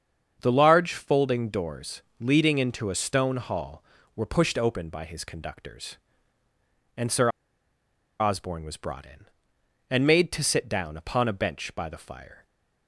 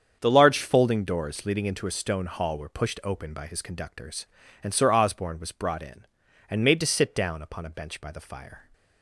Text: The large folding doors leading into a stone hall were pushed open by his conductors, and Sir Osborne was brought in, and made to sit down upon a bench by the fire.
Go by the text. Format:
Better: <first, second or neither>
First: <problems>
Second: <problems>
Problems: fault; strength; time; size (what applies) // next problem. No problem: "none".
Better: second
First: starts louder than the rest; until 1.4 s; 7 dB // pauses between "doors" and "leading"; slight; at 2.0 s; 0.20 s long // pauses between "Sir" and "Osborne"; noticeable; at 7.2 s; 0.91 s long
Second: starts louder than the rest; strong; until 1.2 s; 7.5 dB